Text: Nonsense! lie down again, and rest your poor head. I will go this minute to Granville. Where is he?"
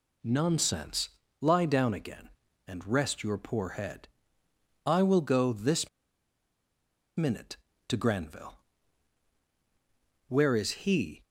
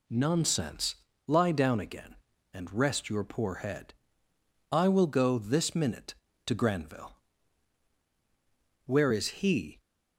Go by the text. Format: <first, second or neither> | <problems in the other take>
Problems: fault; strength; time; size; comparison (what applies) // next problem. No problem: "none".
second | pauses between "this" and "minute"; strong; at 5.8 s; 1.2 s long